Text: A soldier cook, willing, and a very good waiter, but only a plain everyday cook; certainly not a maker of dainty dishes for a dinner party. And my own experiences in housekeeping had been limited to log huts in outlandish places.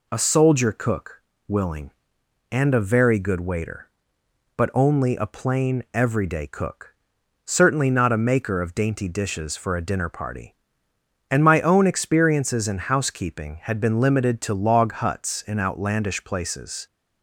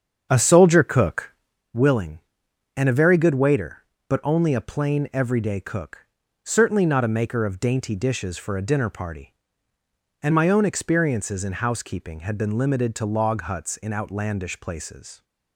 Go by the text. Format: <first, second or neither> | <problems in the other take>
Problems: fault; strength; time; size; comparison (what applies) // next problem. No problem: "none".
first | starts louder than the rest; strong; until 1.6 s; 7.5 dB